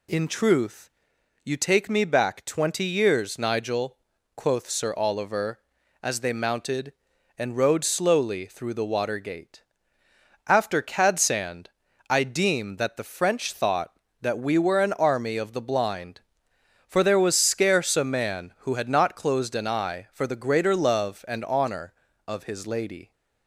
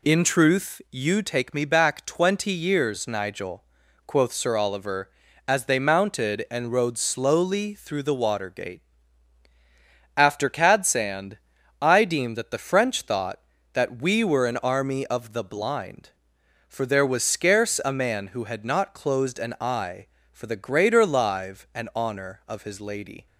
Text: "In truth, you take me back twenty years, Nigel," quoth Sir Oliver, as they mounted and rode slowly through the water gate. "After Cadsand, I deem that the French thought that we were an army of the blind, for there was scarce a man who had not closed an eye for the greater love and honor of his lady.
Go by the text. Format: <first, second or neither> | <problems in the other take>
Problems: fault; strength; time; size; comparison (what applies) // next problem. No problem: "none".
first | says "live" for "love"; at 21.0 s